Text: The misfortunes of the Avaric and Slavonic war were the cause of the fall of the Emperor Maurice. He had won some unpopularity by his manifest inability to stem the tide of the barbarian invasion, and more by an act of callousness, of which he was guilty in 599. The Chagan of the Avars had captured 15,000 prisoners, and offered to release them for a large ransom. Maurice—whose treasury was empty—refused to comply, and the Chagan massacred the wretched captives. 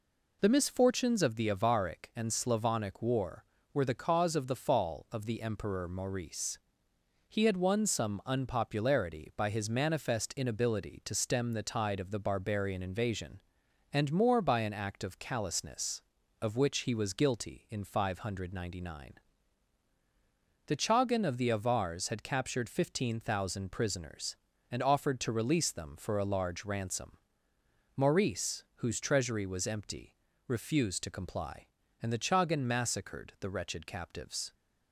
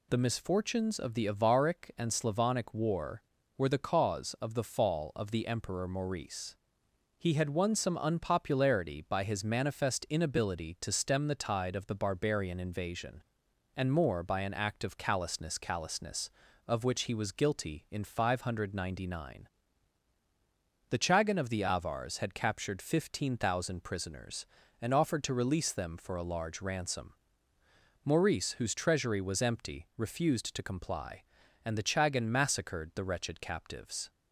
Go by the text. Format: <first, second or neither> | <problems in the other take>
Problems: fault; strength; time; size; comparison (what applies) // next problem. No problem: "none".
first | says "callousness" twice; at 15.5 s